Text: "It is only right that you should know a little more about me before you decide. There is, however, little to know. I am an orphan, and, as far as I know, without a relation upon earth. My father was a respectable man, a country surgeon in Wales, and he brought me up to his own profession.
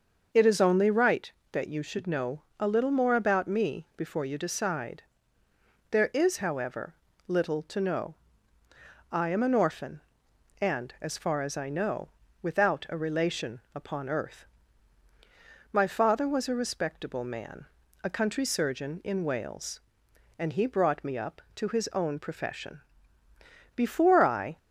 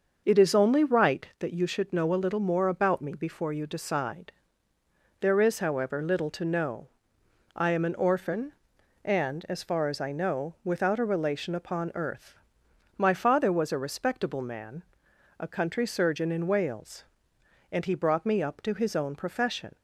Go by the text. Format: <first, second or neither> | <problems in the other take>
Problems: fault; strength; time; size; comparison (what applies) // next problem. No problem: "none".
second | starts louder than the rest; until 1.5 s; 6.5 dB; also in the second // pauses between "know" and "a"; slight; at 2.4 s; 0.16 s long // goes on to say "Before I"; noticeable; from 23.7 s on; 0.82 s long